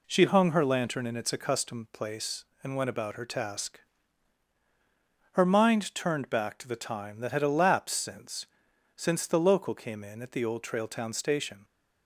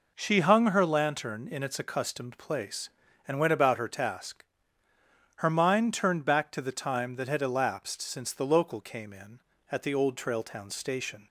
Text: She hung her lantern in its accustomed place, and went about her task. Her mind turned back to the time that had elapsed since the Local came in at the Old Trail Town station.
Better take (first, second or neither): second